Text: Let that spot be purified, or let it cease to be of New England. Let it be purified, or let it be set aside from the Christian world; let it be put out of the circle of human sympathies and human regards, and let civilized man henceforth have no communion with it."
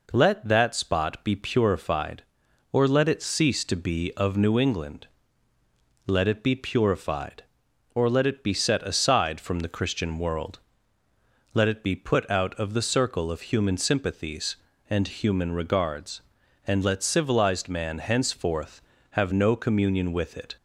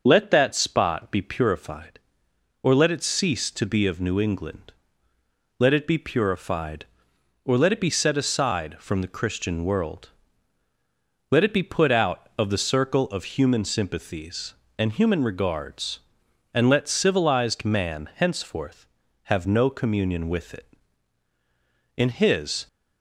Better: first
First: none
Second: starts louder than the rest; noticeable; until 1.0 s; 6 dB // goes on to say "In his"; noticeable; from 21.9 s on; 0.70 s long

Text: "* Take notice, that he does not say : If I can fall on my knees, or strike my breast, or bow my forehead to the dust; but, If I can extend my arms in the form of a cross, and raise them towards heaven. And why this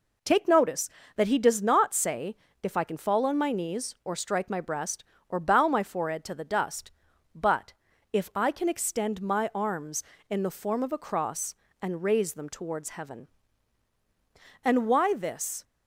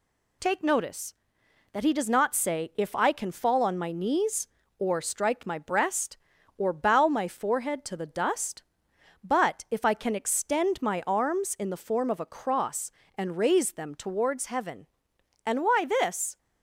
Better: neither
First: none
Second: none

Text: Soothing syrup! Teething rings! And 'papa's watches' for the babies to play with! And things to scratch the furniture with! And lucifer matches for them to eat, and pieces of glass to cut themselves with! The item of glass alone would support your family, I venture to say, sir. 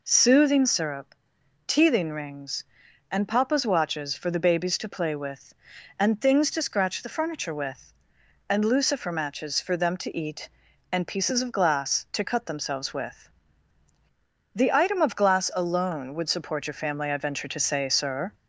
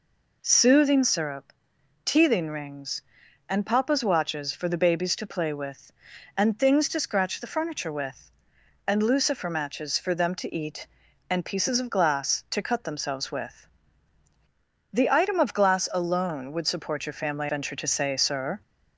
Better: first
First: none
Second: skips "I"; at 17.4 s

